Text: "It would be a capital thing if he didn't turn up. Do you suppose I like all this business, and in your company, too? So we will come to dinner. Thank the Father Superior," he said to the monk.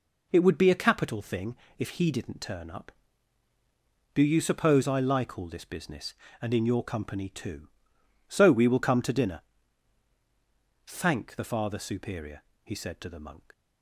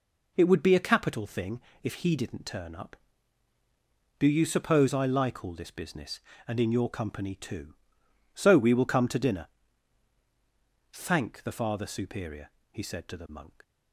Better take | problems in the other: neither | pauses between "thing" and "if"; slight; the same in both

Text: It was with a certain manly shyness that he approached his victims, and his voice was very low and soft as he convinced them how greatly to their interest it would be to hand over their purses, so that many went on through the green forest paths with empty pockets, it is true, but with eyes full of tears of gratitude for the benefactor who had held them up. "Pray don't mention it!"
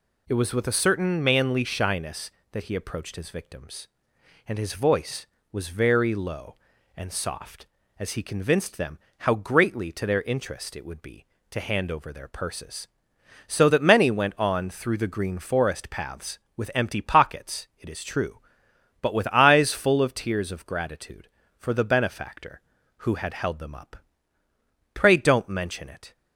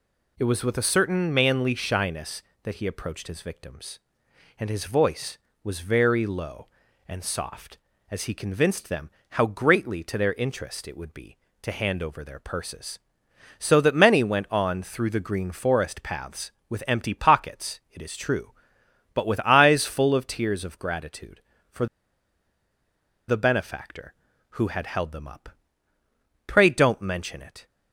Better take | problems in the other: first | pauses between "them" and "how"; slight; at 9.0 s; 0.20 s long; slight in the first // pauses between "for" and "the"; strong; at 21.8 s; 1.4 s long

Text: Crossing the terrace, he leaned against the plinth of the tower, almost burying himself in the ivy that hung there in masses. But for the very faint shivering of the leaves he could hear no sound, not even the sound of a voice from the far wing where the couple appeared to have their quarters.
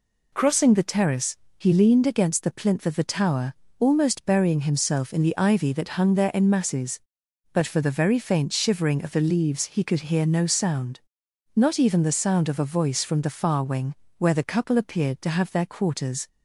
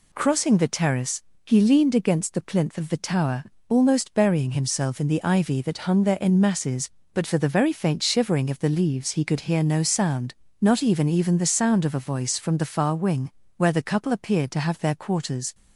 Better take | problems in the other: first | says "even" twice; at 11.0 s // pauses between "wing" and "where"; slight; at 13.3 s; 0.26 s long; slight in the first

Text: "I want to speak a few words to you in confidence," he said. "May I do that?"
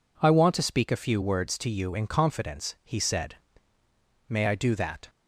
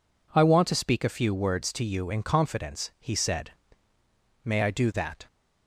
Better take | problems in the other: neither | none

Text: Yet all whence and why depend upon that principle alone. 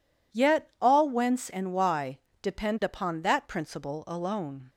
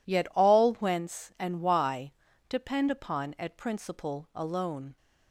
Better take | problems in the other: first | pauses between "why" and "depend"; at 2.1 s; 0.37 s long; slight in the first // says "at" for "that"; at 3.3 s

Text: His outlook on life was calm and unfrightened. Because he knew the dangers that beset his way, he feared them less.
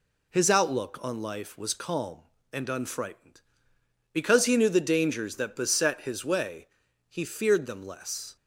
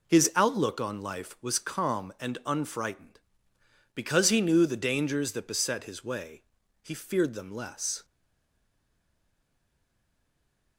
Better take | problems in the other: first | stays silent after the last word; strong; from 8.0 s on; 2.7 s long

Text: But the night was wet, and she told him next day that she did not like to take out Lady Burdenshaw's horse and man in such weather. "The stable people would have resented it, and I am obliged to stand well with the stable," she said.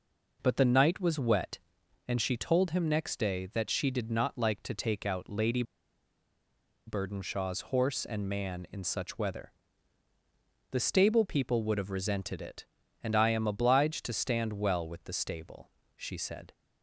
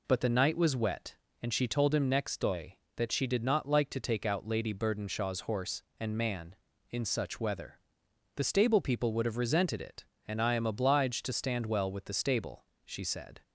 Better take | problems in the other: second | pauses between "Lady" and "Burdenshaw's"; at 5.6 s; 1.2 s long

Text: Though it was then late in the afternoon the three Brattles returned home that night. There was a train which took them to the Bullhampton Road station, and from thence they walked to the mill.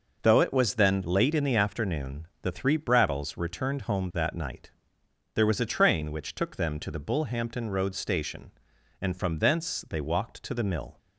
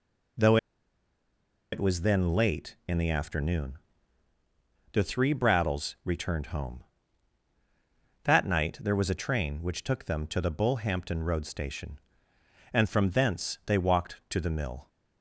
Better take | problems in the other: first | pauses between "Though" and "it"; at 0.5 s; 1.1 s long // pauses between "afternoon" and "the"; at 3.7 s; 1.1 s long; slight in the first

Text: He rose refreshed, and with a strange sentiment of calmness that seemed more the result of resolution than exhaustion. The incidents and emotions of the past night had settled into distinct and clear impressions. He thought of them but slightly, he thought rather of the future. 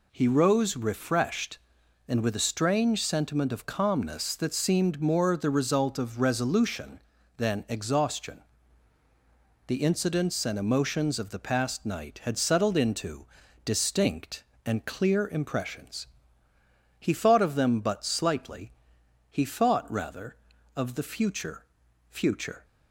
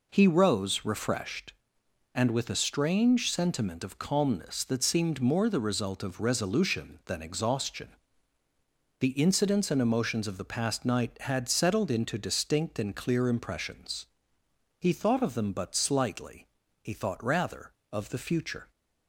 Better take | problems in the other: second | pauses between "into" and "distinct"; at 13.2 s; 0.40 s long // says "future" twice; at 22.0 s

